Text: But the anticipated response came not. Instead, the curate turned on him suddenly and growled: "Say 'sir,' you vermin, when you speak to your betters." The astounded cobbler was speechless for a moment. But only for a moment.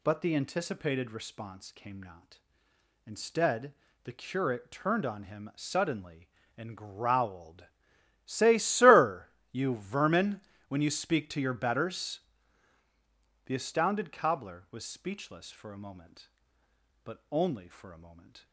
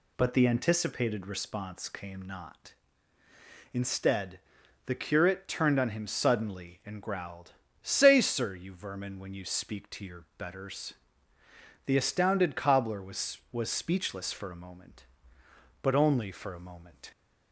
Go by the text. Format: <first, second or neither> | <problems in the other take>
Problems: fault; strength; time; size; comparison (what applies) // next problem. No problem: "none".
first | says "was" twice; at 13.5 s